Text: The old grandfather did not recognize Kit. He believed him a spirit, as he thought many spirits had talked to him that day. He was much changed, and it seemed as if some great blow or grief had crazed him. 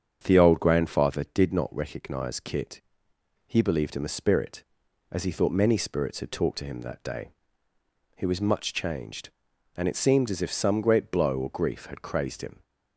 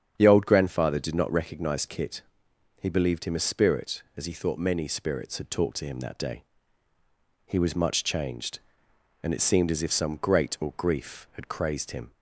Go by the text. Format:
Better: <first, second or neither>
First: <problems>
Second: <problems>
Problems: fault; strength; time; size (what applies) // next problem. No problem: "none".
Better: first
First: starts louder than the rest; strong; until 1.2 s; 7.5 dB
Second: starts louder than the rest; strong; until 1.1 s; 8 dB // skips "blow"; at 10.5 s